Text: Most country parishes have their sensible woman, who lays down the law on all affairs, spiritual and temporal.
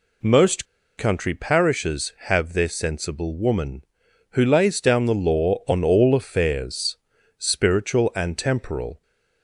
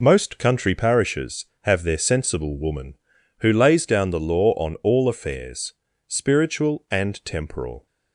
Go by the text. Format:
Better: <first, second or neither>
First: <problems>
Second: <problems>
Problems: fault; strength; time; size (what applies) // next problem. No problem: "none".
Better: second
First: pauses between "Most" and "country"; slight; at 0.6 s; 0.31 s long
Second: none